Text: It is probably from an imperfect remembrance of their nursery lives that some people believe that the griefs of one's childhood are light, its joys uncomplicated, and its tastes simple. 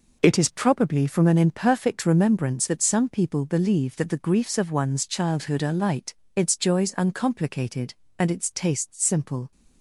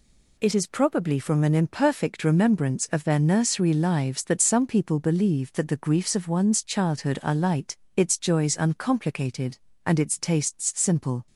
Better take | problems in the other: second | skips "of their nursery lives"; at 2.6 s

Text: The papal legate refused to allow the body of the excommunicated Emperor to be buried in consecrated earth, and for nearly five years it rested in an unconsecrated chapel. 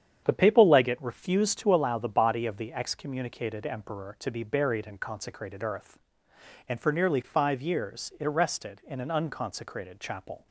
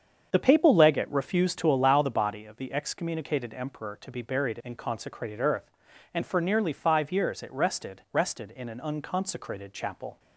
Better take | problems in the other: first | starts louder than the rest; strong; until 1.3 s; 7 dB; strong in the first // says "rested" twice; at 8.1 s

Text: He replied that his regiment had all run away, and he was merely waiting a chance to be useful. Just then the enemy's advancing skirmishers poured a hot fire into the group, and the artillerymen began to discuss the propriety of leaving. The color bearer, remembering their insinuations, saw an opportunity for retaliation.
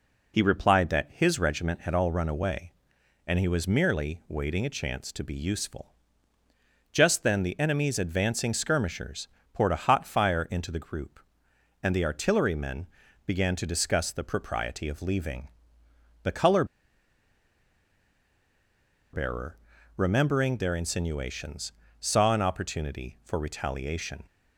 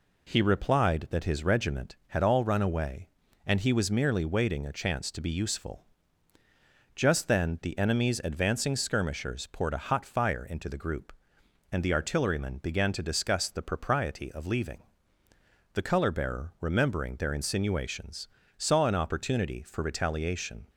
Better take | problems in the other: second | pauses between "skirmishers" and "poured"; slight; at 9.2 s; 0.24 s long // pauses between "artillerymen" and "began"; at 12.8 s; 0.38 s long // pauses between "color" and "bearer"; strong; at 16.6 s; 2.4 s long

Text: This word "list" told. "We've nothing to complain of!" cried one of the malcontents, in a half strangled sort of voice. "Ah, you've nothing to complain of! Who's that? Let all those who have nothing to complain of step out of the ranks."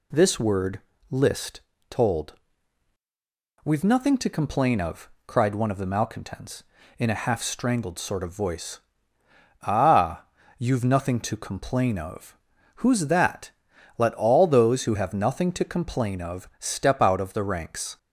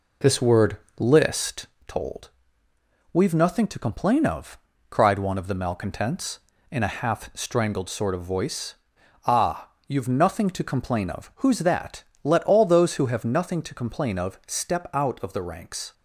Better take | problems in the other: first | starts louder than the rest; noticeable; until 1.7 s; 4 dB // pauses between "word" and "list"; slight; at 0.7 s; 0.24 s long; slight in the first // pauses between "list" and "told"; slight; at 1.6 s; 0.22 s long; slight in the first

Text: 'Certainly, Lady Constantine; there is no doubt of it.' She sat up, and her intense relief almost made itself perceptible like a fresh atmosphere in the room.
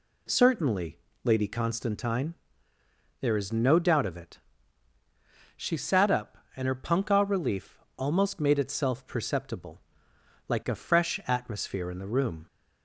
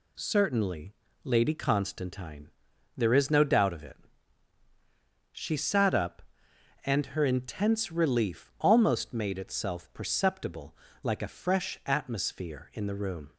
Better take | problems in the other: second | says "punkah" for "intense"; at 6.7 s // pauses between "relief" and "almost"; slight; at 7.7 s; 0.20 s long // pauses between "perceptible" and "like"; noticeable; at 9.8 s; 0.68 s long; slight in the second

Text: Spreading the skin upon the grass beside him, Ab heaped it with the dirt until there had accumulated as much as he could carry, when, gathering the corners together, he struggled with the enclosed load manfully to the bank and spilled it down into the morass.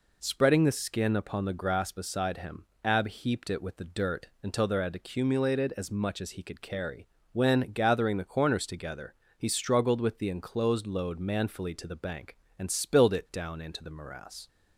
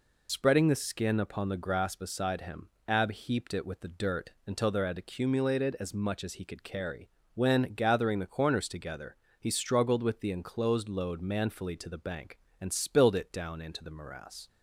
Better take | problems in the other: first | loses the start of "Spreading"; at 0.2 s; 40 ms // pauses between "dirt" and "until"; slight; at 4.3 s; 0.16 s long; slight in the first

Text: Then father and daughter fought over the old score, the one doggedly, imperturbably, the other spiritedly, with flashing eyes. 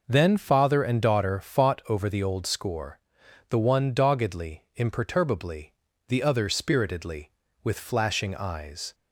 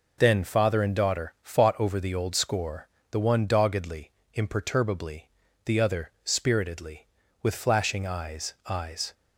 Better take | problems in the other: first | says "eyes" twice; at 8.6 s

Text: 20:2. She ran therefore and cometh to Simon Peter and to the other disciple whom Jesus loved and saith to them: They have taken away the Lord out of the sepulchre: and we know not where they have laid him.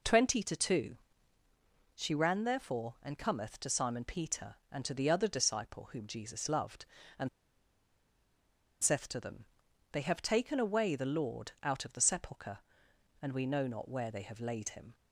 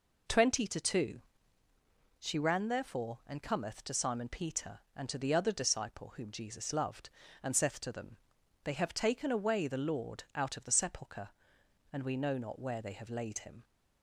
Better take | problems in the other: second | pauses between "and" and "saith"; strong; at 7.2 s; 1.5 s long

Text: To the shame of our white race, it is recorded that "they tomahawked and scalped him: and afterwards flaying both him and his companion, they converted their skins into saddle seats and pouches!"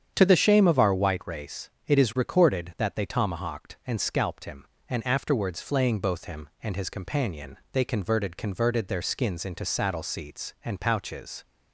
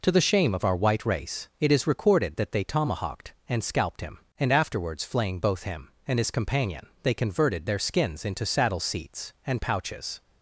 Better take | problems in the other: second | starts louder than the rest; strong; until 1.1 s; 8.5 dB // says "converted" twice; at 8.3 s

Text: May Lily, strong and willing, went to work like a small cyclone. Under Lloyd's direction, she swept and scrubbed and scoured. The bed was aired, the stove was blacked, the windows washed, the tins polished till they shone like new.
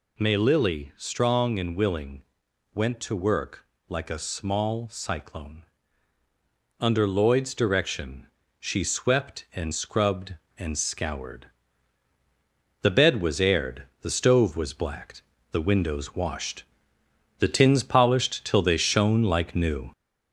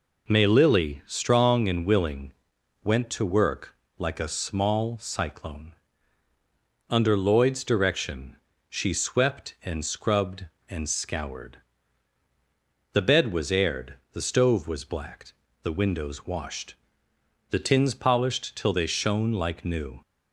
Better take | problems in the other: second | gets louder; noticeable; throughout; 4 dB // pauses between "work" and "like"; slight; at 3.6 s; 0.24 s long; slight in the second

